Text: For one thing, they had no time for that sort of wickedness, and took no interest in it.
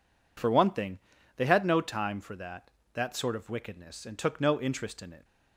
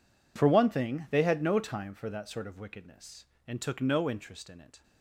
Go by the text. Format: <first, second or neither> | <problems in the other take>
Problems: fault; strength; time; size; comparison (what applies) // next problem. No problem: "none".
second | says "that" twice; at 2.9 s